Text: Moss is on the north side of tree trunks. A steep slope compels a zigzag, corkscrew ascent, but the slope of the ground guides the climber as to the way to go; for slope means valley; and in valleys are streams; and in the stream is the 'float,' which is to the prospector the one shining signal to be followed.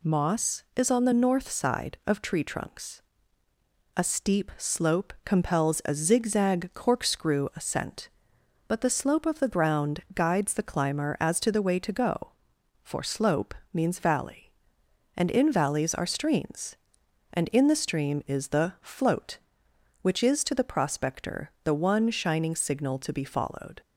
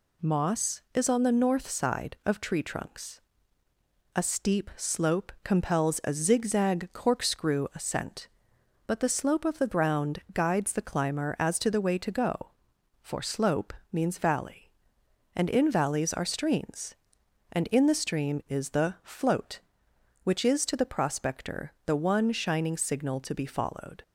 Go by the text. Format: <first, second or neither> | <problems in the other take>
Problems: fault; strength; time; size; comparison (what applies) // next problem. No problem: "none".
neither | pauses between "slope" and "means"; slight; the same in both